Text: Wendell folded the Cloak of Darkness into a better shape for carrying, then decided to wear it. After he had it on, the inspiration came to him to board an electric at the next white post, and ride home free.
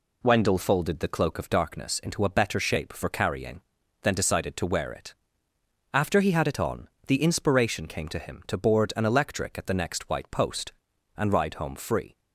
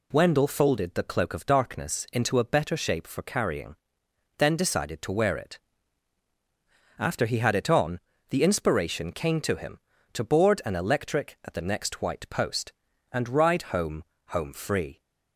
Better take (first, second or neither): first